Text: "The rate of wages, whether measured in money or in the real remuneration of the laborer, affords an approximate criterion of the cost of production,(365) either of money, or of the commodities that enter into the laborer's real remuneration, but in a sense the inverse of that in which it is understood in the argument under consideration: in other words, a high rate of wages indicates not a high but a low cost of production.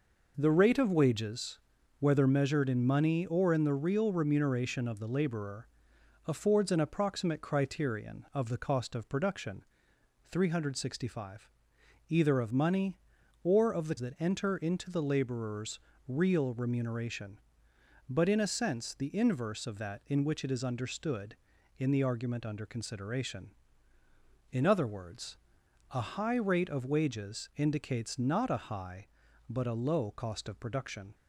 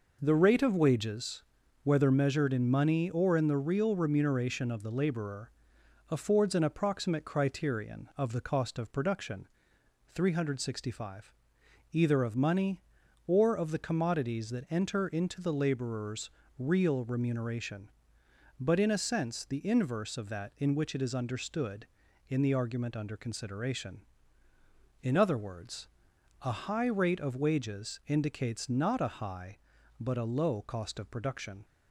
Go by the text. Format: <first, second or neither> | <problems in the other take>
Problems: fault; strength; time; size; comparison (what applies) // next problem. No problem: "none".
second | skips "commodities"; at 13.9 s // pauses between "laborer's" and "real"; slight; at 15.7 s; 0.28 s long; slight in the second